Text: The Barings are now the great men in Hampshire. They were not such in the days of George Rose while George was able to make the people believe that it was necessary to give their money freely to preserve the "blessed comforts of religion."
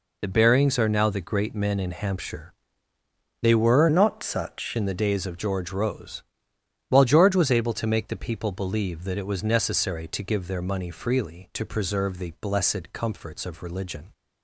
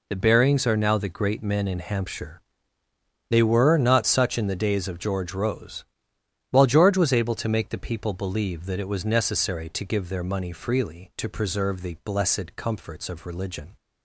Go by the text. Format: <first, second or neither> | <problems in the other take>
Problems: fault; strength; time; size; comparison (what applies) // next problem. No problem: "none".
second | changes voice from "not" to "such"; from 3.8 to 4.7 s; 0.9 s long // pauses between "Rose" and "while"; noticeable; at 6.2 s; 0.66 s long; noticeable in the second